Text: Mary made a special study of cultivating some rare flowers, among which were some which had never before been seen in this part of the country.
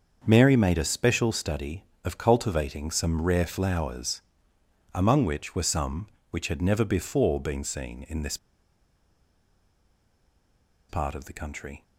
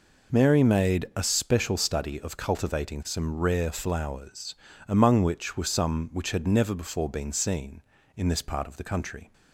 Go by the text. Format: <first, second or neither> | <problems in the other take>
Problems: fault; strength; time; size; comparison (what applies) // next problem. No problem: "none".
second | starts louder than the rest; until 1.2 s; 6.5 dB // pauses between "this" and "part"; strong; at 8.3 s; 2.5 s long